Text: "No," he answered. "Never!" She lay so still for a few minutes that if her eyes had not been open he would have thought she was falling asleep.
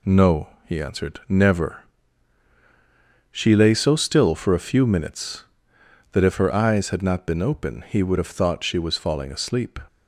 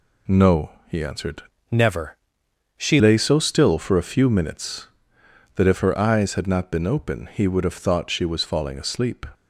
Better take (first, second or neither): first